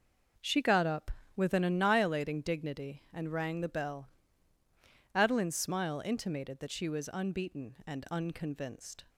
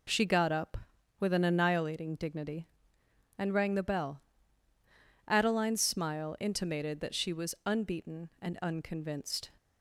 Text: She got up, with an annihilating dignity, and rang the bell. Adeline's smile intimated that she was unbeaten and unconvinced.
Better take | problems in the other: neither | none

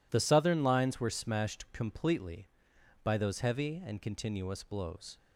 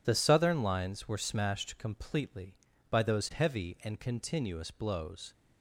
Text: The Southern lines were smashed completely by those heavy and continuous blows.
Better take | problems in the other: neither | none

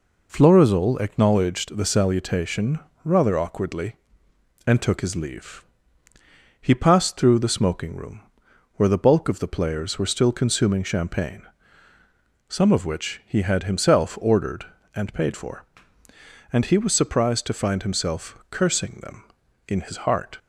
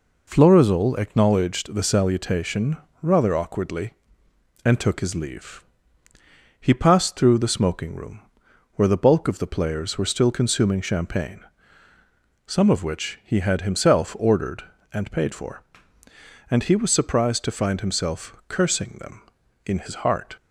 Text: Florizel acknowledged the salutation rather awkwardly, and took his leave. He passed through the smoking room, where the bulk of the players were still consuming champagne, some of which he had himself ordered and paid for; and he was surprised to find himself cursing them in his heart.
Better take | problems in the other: neither | pauses between "salutation" and "rather"; slight; the same in both

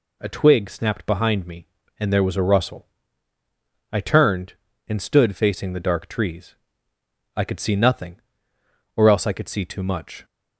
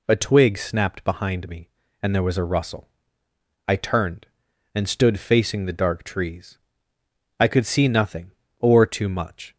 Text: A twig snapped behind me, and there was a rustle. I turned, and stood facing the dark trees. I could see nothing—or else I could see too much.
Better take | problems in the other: first | skips "else I could see"; at 8.8 s

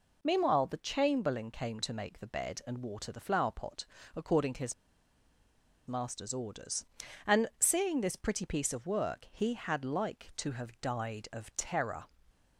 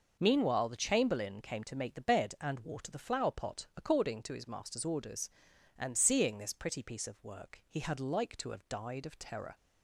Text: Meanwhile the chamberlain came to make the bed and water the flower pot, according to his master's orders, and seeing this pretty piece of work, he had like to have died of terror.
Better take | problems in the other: second | pauses between "his" and "master's"; at 4.7 s; 1.1 s long

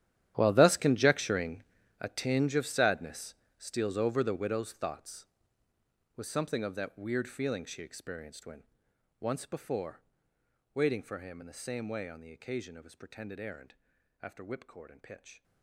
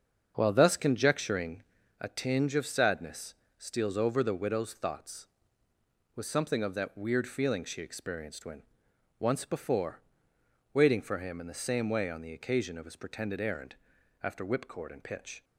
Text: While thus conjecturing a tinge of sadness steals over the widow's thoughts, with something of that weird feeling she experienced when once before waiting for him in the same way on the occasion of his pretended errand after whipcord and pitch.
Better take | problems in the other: second | gets quieter; strong; throughout; 17.5 dB // starts louder than the rest; strong; until 1.3 s; 11.5 dB; also in the second // pauses between "conjecturing" and "a"; at 1.6 s; 0.40 s long; also in the second // pauses between "sadness" and "steals"; slight; at 3.3 s; 0.22 s long; slight in the second // pauses between "when" and "once"; noticeable; at 8.6 s; 0.56 s long; noticeable in the second // pauses between "before" and "waiting"; noticeable; at 10.0 s; 0.74 s long; noticeable in the second // pauses between "errand" and "after"; noticeable; at 13.7 s; 0.48 s long; noticeable in the second

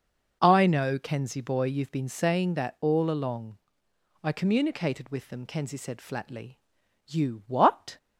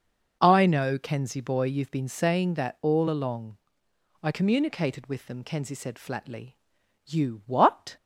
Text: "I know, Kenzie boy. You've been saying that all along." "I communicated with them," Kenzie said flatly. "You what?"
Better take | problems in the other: neither | none

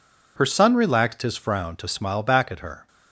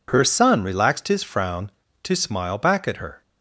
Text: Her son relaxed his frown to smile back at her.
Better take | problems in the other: neither | none

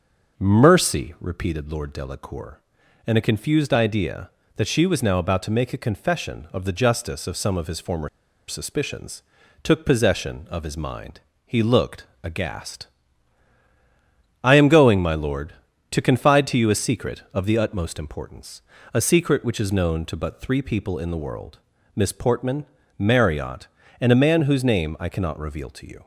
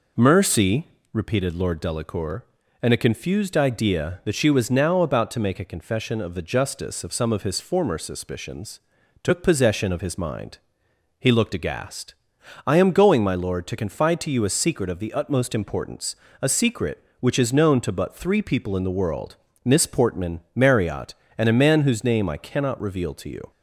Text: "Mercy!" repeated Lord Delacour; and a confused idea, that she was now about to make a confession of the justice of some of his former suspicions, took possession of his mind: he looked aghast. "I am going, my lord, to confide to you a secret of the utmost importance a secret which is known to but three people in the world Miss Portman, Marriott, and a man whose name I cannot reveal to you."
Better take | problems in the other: second | starts louder than the rest; noticeable; until 1.4 s; 6 dB // pauses between "former" and "suspicions"; at 8.0 s; 0.40 s long // pauses between "looked" and "aghast"; slight; at 12.0 s; 0.18 s long // pauses between "importance" and "a"; slight; at 18.6 s; 0.32 s long; slight in the second // pauses between "world" and "Miss"; slight; at 21.5 s; 0.36 s long; slight in the second

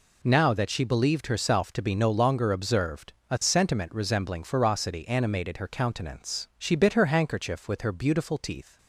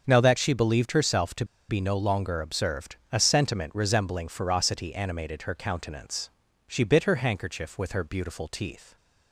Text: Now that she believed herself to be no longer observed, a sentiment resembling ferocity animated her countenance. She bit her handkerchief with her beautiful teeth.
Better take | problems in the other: first | starts louder than the rest; until 1.0 s; 7 dB // pauses between "to" and "be"; slight; at 1.4 s; 0.23 s long

